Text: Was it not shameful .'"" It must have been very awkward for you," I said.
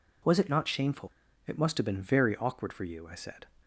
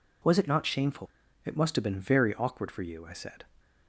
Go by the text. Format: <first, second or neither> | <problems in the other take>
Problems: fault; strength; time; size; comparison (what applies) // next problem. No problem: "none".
neither | none